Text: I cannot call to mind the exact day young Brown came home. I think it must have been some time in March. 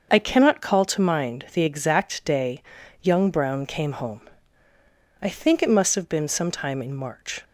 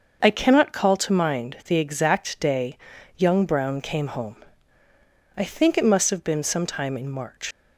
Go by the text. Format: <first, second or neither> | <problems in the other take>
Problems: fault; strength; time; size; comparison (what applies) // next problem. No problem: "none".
first | starts louder than the rest; until 1.2 s; 6 dB; also in the first // pauses between "day" and "young"; at 2.7 s; 0.40 s long; also in the first // leaves "March" unfinished; at 7.5 s; 75 ms